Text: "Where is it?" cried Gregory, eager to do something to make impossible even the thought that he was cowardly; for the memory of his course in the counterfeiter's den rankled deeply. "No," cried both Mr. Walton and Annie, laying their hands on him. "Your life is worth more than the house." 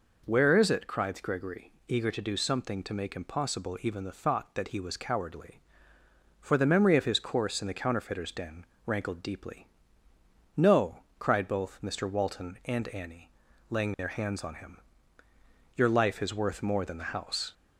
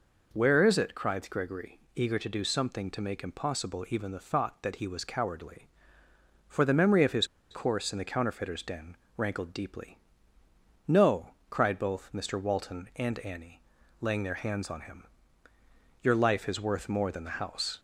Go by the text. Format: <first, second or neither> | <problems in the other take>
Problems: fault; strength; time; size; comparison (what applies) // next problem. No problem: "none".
first | pauses between "his" and "course"; slight; at 7.2 s; 0.24 s long // pauses between "den" and "rankled"; slight; at 8.9 s; 0.22 s long; slight in the first